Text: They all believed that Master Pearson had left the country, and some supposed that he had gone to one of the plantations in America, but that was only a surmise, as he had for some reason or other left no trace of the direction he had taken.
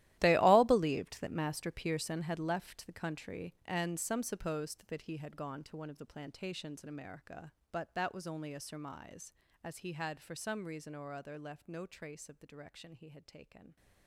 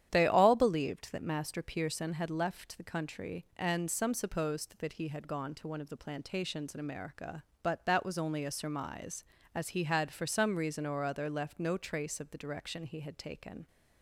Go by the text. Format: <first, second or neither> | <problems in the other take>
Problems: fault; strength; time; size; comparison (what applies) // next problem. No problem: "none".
second | gets quieter; strong; throughout; 17 dB // starts louder than the rest; strong; until 1.2 s; 15 dB; strong in the second